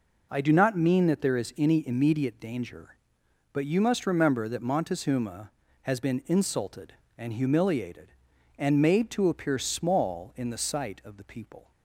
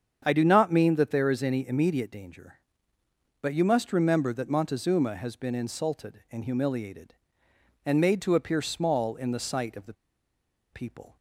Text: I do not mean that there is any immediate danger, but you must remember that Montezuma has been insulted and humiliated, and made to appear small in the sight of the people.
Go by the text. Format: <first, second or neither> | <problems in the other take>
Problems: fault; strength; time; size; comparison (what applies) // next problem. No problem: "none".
first | starts louder than the rest; strong; until 1.2 s; 7.5 dB // pauses between "the" and "people"; noticeable; at 9.9 s; 0.79 s long